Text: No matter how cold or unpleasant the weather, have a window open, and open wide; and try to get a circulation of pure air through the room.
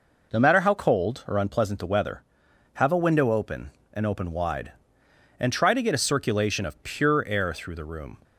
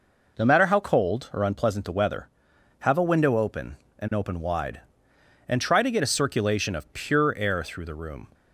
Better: neither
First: none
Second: none

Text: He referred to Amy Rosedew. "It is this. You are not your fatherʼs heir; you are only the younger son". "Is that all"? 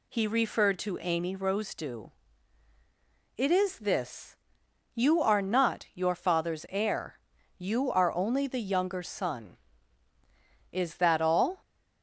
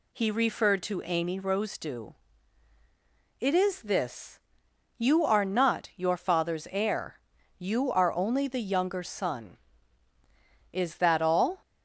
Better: neither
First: none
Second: none

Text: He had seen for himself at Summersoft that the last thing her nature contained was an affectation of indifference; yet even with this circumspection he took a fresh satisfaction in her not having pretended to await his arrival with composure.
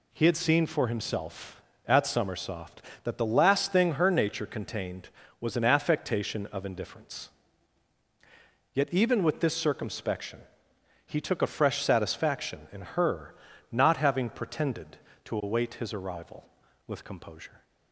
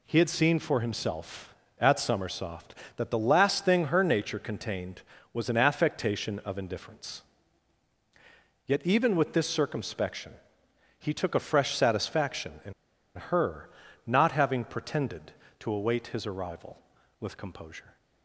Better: first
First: pauses between "circumspection" and "he"; noticeable; at 10.3 s; 0.66 s long // pauses between "her" and "not"; at 13.3 s; 0.38 s long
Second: pauses between "circumspection" and "he"; noticeable; at 10.3 s; 0.66 s long // pauses between "in" and "her"; at 12.7 s; 0.43 s long // pauses between "her" and "not"; at 13.6 s; 0.38 s long

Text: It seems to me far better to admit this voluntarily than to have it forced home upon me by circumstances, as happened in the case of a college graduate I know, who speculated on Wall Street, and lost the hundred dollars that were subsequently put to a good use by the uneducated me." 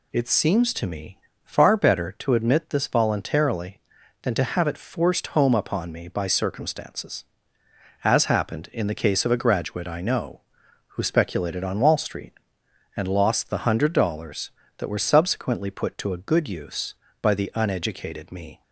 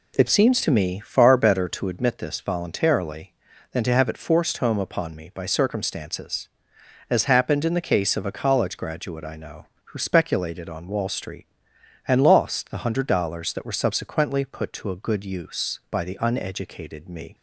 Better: second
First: pauses between "me" and "far"; slight; at 1.1 s; 0.24 s long // skips "college"; at 9.3 s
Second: none

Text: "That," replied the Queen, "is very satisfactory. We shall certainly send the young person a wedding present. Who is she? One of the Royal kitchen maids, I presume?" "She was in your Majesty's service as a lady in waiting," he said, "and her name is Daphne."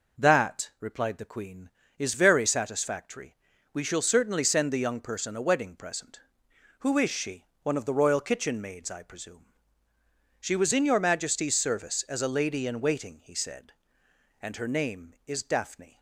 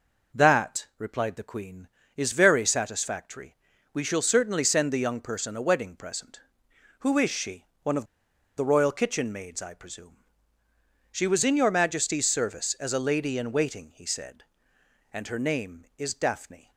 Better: first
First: none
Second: pauses between "of" and "the"; noticeable; at 8.0 s; 0.51 s long

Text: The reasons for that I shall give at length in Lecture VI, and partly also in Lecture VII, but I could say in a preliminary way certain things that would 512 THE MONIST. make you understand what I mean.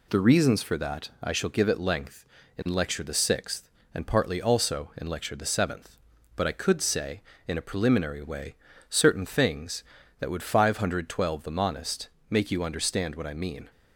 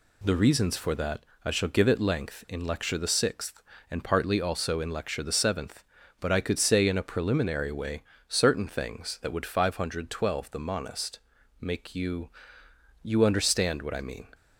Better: first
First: pauses between "way" and "certain"; slight; at 8.5 s; 0.36 s long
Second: pauses between "that" and "I"; slight; at 1.2 s; 0.20 s long // pauses between "way" and "certain"; slight; at 8.0 s; 0.26 s long // says "you" twice; at 13.0 s

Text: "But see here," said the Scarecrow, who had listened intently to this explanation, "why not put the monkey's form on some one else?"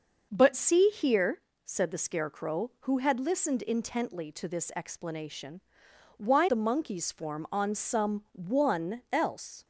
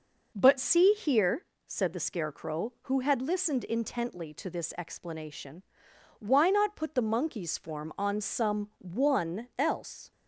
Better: second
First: skips "not put"; at 6.4 s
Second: none

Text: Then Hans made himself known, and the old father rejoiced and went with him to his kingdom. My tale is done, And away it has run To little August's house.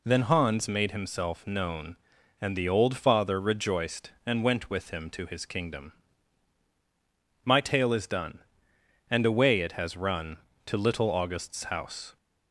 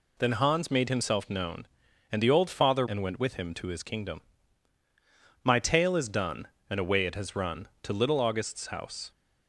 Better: first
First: none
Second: skips "rejoiced"; at 2.8 s

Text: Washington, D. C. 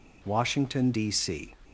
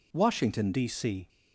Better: first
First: none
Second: changes voice at "D"; from 0.7 s on; 0.5 s long

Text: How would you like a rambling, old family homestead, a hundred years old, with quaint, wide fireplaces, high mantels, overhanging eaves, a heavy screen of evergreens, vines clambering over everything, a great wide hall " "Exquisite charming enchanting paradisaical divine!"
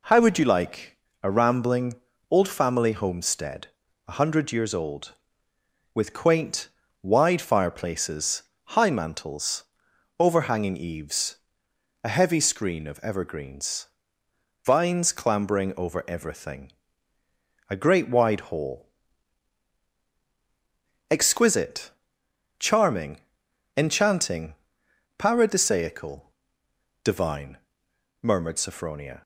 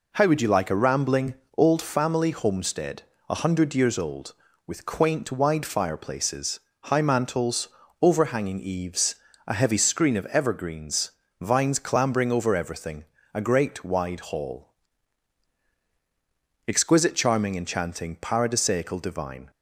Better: second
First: pauses between "like" and "a"; slight; at 0.9 s; 0.24 s long // pauses between "Exquisite" and "charming"; noticeable; at 21.9 s; 0.66 s long // pauses between "charming" and "enchanting"; noticeable; at 23.2 s; 0.52 s long // pauses between "enchanting" and "paradisaical"; noticeable; at 24.5 s; 0.64 s long // pauses between "paradisaical" and "divine"; noticeable; at 26.2 s; 0.74 s long // goes on to say "murmured Sophronia"; noticeable; from 28.2 s on; 1.0 s long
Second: none

